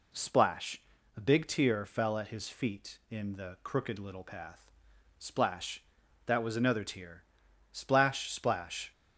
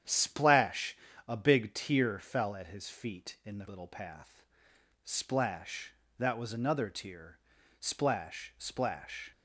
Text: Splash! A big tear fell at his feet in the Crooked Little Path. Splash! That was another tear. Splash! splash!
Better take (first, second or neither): first